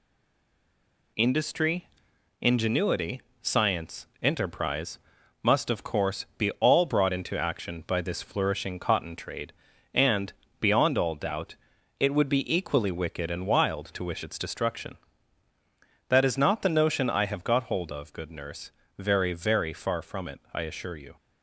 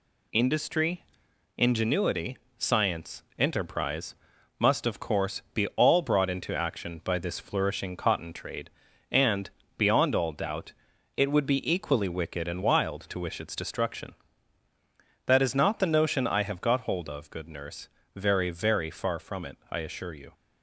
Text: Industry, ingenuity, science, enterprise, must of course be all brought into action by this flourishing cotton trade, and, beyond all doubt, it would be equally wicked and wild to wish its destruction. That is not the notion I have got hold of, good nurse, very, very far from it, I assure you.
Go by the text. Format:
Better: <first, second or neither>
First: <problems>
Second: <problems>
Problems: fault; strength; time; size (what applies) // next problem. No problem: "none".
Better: second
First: stays silent before the first word; until 1.1 s; 1.1 s long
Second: none